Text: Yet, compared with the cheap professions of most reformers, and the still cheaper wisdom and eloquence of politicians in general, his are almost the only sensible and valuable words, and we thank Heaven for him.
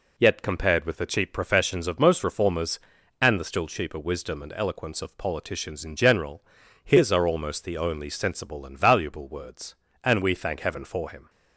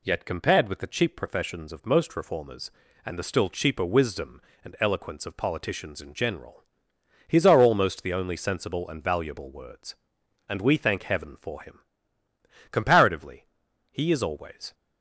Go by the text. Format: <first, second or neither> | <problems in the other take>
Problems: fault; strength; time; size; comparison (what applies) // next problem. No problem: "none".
first | goes on to say "Comparatively he is always"; strong; from 12.7 s on; 2.0 s long